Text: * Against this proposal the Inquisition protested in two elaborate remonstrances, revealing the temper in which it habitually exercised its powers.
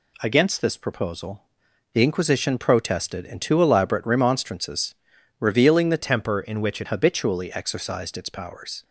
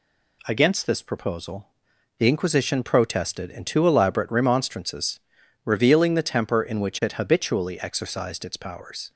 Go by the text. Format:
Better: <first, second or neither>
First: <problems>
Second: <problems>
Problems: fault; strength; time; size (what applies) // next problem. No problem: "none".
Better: second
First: pauses between "proposal" and "the"; noticeable; at 1.4 s; 0.50 s long // changes voice from "temper" to "it"; from 5.9 to 6.8 s; 0.9 s long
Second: pauses between "proposal" and "the"; noticeable; at 1.6 s; 0.50 s long